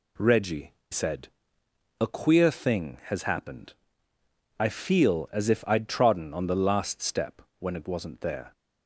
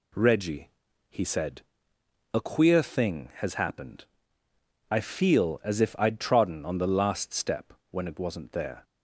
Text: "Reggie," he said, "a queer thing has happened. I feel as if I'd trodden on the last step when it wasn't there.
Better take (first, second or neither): second